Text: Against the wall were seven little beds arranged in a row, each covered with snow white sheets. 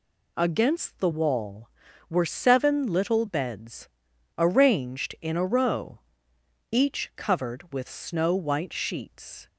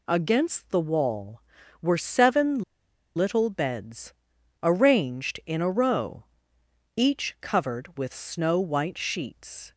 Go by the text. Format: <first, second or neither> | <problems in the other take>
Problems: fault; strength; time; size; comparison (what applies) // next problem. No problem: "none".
first | pauses between "seven" and "little"; noticeable; at 2.6 s; 0.52 s long // pauses between "beds" and "arranged"; noticeable; at 4.1 s; 0.48 s long; noticeable in the first